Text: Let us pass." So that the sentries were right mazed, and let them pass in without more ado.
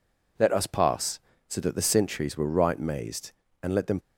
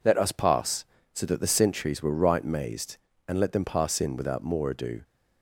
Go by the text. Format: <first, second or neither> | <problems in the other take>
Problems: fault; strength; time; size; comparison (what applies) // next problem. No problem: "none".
second | stops before "pass in without more ado"; at 4.0 s